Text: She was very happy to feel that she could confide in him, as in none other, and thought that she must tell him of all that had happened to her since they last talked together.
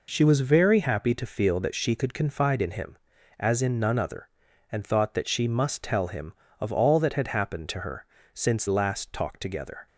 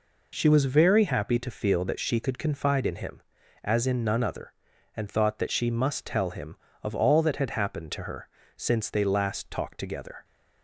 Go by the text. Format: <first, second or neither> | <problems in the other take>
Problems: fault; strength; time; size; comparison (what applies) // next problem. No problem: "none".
second | pauses between "her" and "since"; slight; at 8.0 s; 0.28 s long; slight in the second // skips "they"; at 8.6 s